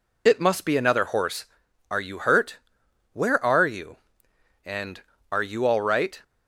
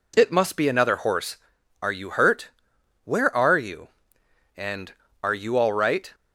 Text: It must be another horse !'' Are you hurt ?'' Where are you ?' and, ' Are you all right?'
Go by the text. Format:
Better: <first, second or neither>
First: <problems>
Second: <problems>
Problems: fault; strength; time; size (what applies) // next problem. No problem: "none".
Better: second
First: loses the start of "It"; at 0.2 s; 35 ms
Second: none